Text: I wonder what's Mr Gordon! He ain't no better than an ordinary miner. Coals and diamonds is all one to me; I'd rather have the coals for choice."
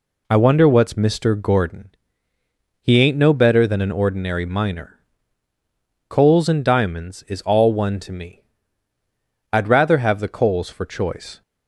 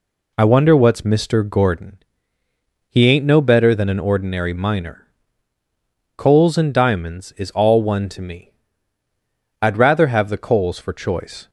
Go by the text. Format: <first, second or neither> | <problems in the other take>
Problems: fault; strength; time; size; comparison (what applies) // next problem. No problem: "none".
neither | none